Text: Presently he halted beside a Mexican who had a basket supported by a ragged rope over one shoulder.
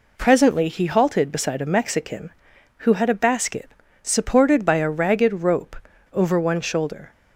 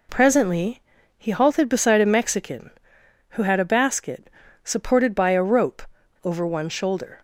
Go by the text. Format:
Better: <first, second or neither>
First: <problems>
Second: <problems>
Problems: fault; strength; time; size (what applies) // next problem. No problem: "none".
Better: first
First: pauses between "basket" and "supported"; slight; at 3.6 s; 0.32 s long // pauses between "rope" and "over"; at 5.7 s; 0.37 s long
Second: pauses between "Presently" and "he"; at 0.8 s; 0.38 s long // pauses between "basket" and "supported"; slight; at 4.2 s; 0.36 s long // skips "ragged"; at 5.4 s // pauses between "rope" and "over"; at 5.8 s; 0.40 s long